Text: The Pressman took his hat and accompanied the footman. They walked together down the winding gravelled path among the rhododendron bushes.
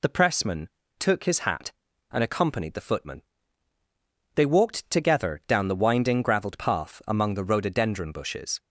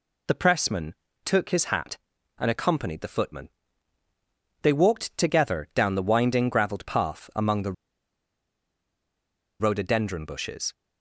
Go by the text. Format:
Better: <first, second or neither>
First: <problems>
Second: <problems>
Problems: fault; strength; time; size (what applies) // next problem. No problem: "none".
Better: first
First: pauses between "Pressman" and "took"; slight; at 0.6 s; 0.30 s long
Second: pauses between "Pressman" and "took"; slight; at 0.9 s; 0.30 s long // pauses between "the" and "rhododendron"; strong; at 7.7 s; 1.8 s long